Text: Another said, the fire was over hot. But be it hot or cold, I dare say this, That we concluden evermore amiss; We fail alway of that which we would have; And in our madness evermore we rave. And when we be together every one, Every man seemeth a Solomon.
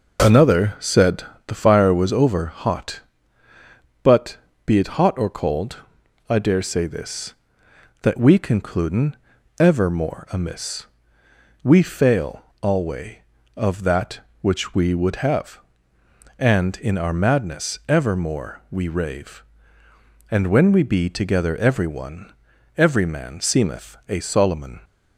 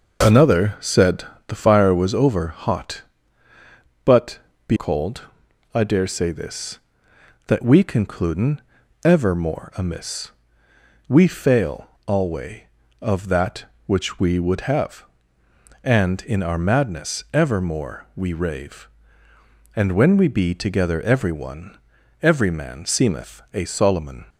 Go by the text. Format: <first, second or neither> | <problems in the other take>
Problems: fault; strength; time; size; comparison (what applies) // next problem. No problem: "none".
first | pauses between "But" and "be"; slight; at 4.3 s; 0.30 s long; slight in the first // skips "it hot or"; at 4.7 s // pauses between "concluden" and "evermore"; at 8.6 s; 0.42 s long; also in the first // pauses between "fail" and "alway"; slight; at 11.8 s; 0.20 s long; slight in the first